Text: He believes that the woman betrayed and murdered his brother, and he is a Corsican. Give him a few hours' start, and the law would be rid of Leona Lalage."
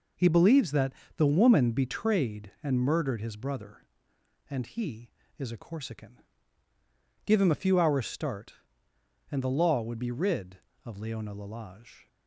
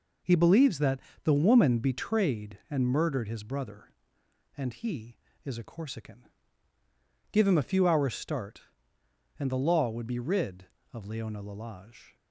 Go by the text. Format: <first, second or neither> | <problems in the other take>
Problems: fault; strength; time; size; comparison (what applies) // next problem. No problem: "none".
neither | pauses between "that" and "the"; slight; the same in both